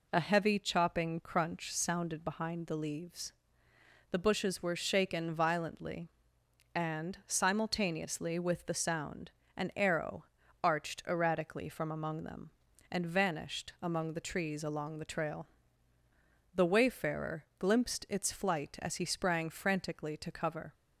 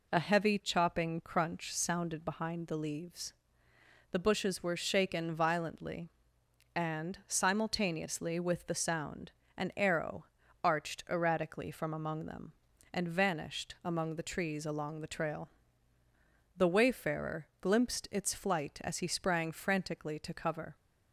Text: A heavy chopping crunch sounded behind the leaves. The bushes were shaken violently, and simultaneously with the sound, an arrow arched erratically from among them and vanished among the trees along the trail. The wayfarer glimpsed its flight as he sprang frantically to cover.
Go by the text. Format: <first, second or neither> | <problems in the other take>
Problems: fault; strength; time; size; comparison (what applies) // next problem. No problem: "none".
neither | pauses between "arrow" and "arched"; the same in both // pauses between "wayfarer" and "glimpsed"; slight; the same in both